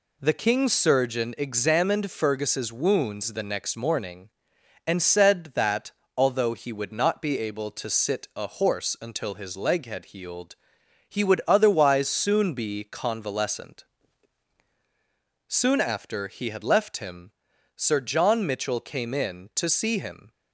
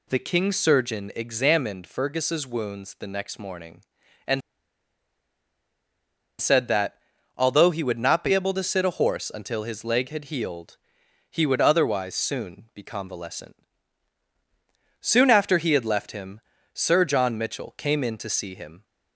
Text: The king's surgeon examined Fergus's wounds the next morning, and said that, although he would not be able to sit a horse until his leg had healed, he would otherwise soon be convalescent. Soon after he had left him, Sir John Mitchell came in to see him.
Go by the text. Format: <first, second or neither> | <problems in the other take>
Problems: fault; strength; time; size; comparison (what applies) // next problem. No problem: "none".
first | pauses between "and" and "said"; strong; at 4.4 s; 2.0 s long